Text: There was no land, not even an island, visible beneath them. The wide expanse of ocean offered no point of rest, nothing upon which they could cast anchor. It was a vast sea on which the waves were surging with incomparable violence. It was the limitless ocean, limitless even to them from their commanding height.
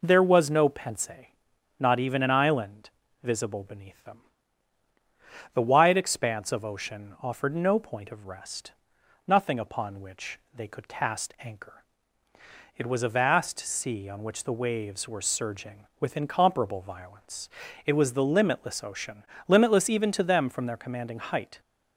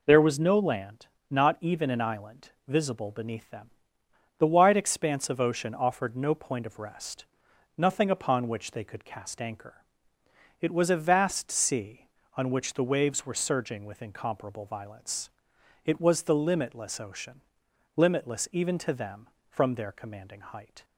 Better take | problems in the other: second | says "pense" for "land"; at 0.6 s // pauses between "which" and "they"; slight; at 10.3 s; 0.16 s long

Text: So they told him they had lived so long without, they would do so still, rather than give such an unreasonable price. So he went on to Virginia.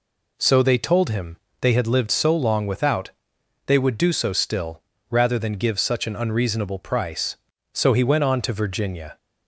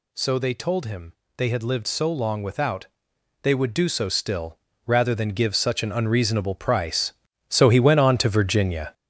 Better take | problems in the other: first | gets louder; strong; throughout; 7.5 dB // pauses between "him" and "they"; slight; at 1.1 s; 0.24 s long; slight in the first

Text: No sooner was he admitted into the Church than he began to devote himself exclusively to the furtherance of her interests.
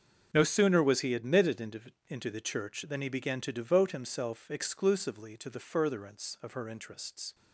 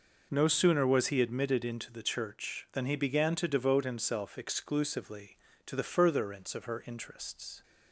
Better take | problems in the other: second | starts louder than the rest; until 1.3 s; 6.5 dB // says "into" twice; at 2.0 s

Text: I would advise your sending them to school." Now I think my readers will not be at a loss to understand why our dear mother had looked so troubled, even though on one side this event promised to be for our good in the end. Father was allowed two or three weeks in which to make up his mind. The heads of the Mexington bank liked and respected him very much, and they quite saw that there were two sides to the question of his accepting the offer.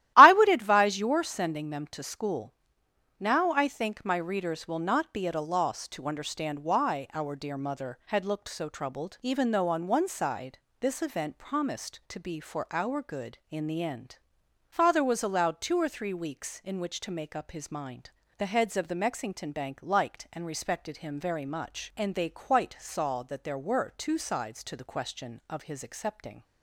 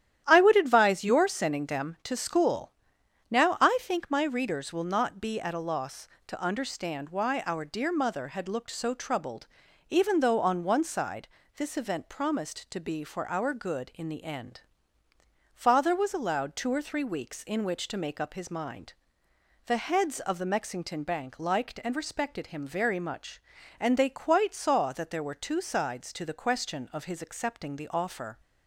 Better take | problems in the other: second | starts louder than the rest; strong; until 1.1 s; 14.5 dB; strong in the second // pauses between "side" and "this"; slight; at 10.5 s; 0.24 s long; slight in the second // stops before "the offer"; at 26.4 s

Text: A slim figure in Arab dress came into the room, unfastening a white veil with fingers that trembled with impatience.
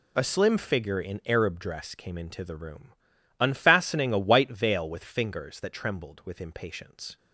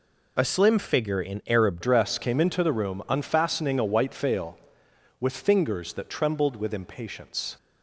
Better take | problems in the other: first | changes voice at "dress"; from 1.8 s on; 5.7 s long

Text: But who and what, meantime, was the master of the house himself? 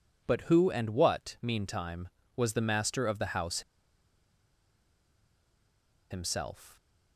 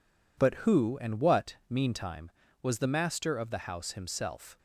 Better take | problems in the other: second | pauses between "house" and "himself"; strong; at 3.6 s; 2.4 s long

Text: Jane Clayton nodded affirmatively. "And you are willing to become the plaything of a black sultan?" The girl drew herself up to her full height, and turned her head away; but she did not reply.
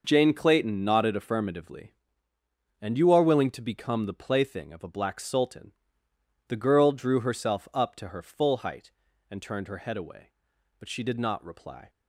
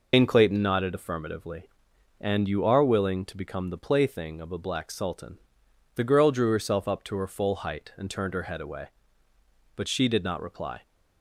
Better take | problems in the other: first | loses the start of "Jane"; at 0.1 s; 120 ms

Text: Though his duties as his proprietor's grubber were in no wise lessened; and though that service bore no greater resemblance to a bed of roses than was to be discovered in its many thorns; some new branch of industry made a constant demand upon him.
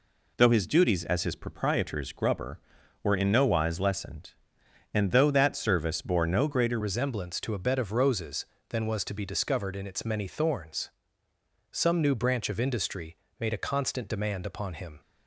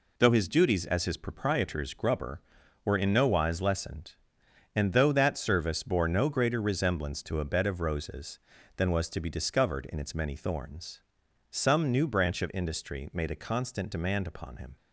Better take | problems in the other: second | changes voice at "resemblance"; from 6.8 s on; 8.2 s long // pauses between "industry" and "made"; slight; at 13.1 s; 0.24 s long

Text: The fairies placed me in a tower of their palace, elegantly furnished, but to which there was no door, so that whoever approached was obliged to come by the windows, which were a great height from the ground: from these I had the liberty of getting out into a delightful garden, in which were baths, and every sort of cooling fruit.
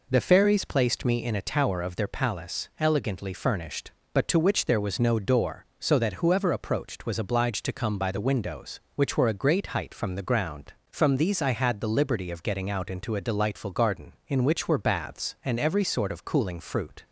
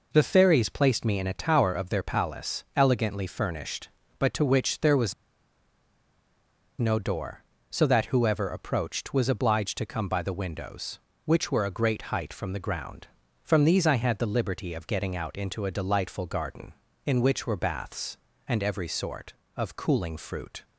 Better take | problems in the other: first | pauses between "was" and "no"; strong; at 5.1 s; 1.6 s long

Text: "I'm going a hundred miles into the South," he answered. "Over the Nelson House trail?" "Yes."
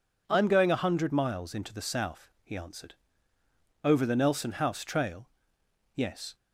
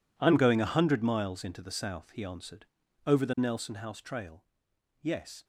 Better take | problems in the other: first | gets quieter; strong; throughout; 17.5 dB

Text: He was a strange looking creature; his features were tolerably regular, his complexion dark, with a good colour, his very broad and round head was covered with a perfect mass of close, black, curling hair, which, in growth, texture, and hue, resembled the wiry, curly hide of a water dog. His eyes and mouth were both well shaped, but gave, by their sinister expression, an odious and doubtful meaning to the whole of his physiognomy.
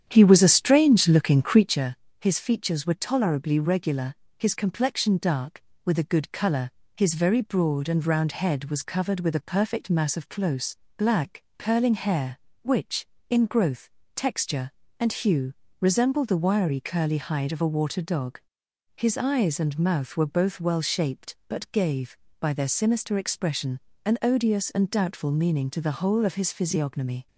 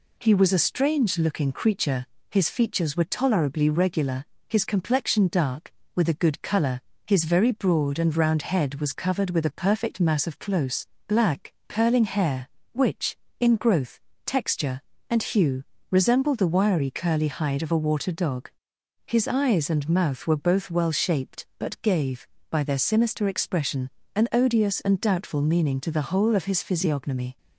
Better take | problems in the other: second | starts louder than the rest; strong; until 1.8 s; 9 dB

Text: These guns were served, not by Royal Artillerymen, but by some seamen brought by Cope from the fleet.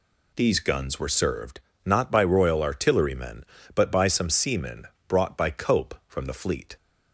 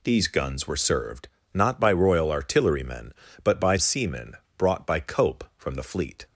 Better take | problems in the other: first | skips "some"; at 3.7 s // pauses between "seamen" and "brought"; slight; at 4.3 s; 0.20 s long; slight in the first

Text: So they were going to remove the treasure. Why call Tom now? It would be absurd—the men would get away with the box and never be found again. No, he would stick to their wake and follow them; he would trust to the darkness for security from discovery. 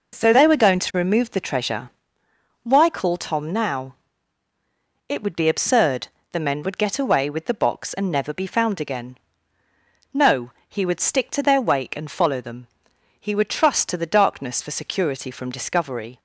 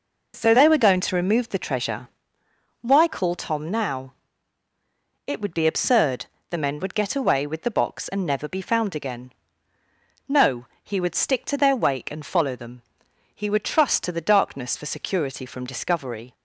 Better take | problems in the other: neither | none

